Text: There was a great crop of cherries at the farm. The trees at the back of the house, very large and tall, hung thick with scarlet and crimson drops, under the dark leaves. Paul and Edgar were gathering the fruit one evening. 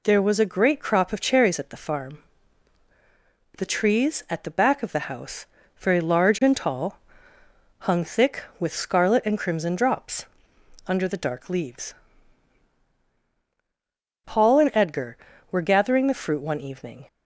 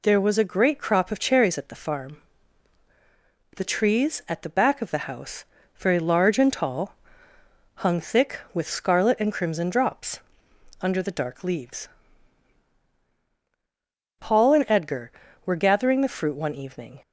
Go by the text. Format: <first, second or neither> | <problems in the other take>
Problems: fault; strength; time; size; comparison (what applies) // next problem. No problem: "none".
neither | none